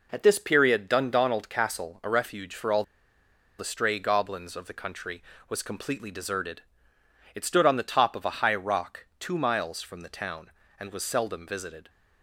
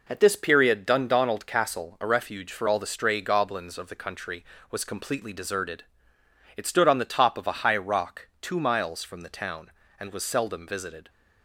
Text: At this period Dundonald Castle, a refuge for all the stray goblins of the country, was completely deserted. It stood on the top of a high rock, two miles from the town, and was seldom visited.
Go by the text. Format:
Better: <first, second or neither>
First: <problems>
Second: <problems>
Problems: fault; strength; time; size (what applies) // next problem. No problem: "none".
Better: second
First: pauses between "all" and "the"; noticeable; at 2.8 s; 0.75 s long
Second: none